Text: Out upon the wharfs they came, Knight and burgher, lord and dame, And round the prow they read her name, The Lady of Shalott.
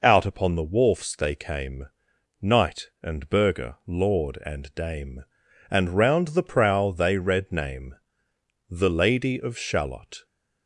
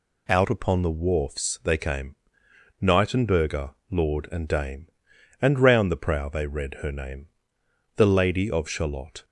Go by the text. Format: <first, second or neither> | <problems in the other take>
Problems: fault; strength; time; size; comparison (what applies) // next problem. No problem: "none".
second | skips "her"; at 7.5 s